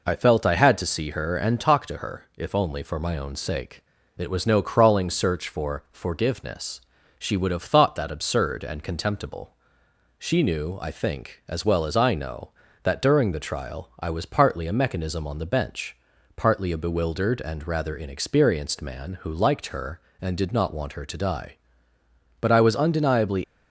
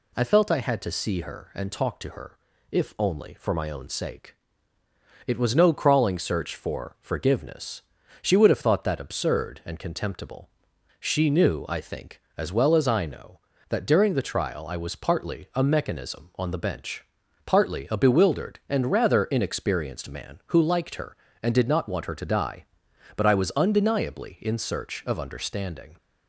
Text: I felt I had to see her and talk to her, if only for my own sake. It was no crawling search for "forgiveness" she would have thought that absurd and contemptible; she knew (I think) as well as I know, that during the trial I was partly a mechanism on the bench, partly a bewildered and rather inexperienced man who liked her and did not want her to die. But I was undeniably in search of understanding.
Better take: second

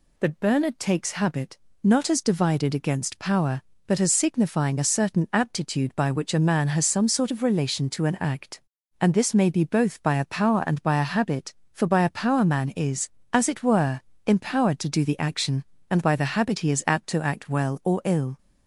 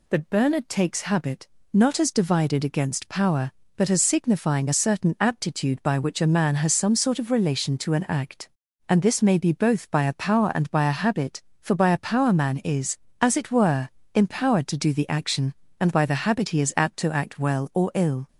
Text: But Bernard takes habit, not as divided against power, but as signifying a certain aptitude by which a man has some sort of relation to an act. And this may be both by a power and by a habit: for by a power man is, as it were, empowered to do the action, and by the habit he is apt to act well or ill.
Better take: neither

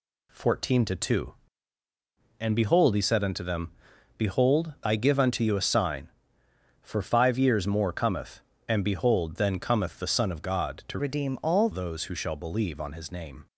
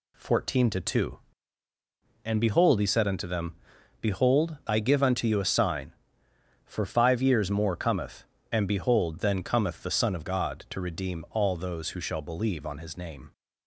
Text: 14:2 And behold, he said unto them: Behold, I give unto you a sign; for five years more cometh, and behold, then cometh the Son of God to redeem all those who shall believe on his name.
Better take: second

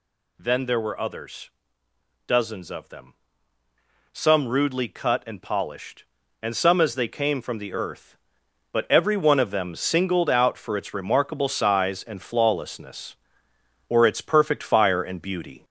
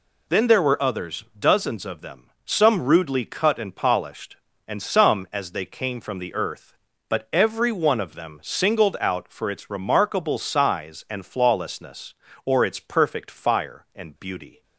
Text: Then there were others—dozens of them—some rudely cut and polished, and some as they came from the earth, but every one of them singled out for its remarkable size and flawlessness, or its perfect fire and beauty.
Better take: second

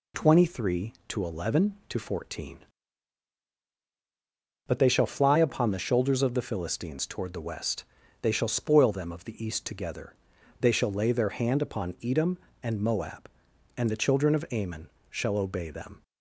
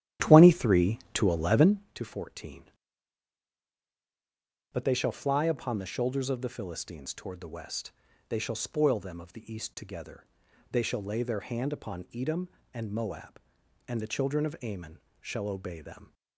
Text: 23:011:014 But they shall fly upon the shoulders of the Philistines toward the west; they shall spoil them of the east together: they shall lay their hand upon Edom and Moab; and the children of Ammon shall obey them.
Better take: first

